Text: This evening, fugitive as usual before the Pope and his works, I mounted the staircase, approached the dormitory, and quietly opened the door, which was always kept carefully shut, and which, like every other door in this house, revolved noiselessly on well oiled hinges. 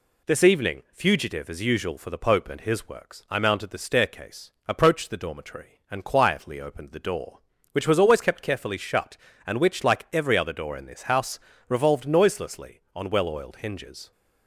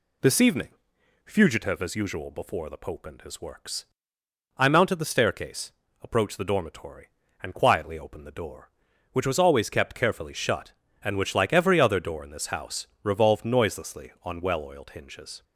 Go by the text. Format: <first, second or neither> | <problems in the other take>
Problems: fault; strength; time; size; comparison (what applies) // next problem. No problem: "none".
second | says "for" for "before"; at 1.9 s